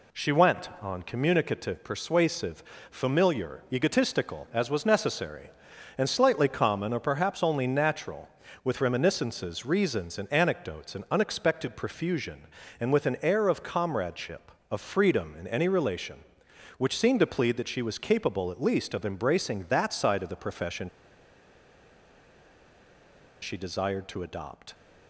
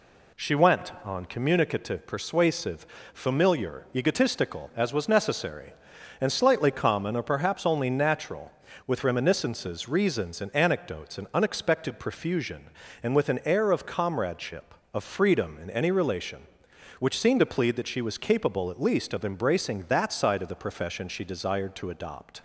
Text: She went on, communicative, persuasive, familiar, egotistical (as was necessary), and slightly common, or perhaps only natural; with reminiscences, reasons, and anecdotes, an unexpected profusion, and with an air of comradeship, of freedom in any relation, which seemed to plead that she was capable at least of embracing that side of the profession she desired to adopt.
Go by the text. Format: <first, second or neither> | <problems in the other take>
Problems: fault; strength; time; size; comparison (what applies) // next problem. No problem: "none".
second | pauses between "profession" and "she"; strong; at 20.8 s; 2.5 s long